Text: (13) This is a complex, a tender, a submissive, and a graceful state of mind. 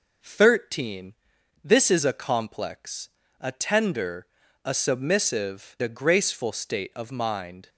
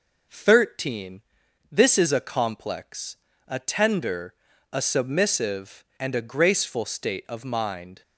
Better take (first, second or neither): second